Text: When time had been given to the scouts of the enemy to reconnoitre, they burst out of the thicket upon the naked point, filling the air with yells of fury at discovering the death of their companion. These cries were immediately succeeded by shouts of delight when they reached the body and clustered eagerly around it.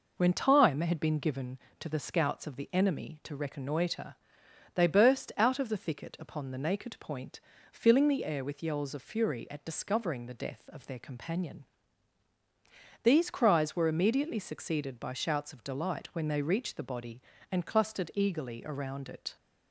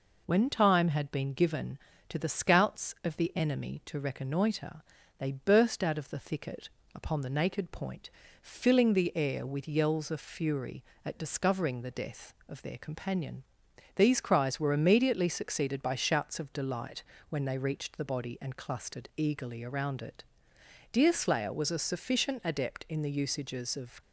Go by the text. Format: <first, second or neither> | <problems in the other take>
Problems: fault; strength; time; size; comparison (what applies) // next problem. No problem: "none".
first | pauses between "thicket" and "upon"; slight; at 6.6 s; 0.26 s long // pauses between "delight" and "when"; slight; at 17.0 s; 0.26 s long // goes on to say "Deerslayer was a sufficient adept in the usages of"; strong; from 20.9 s on; 3.1 s long